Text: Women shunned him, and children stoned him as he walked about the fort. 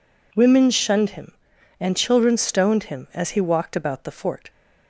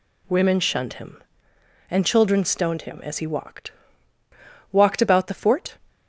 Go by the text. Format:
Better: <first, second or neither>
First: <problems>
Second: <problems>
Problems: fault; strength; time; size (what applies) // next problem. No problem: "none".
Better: first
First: none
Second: says "walked" twice; at 4.7 s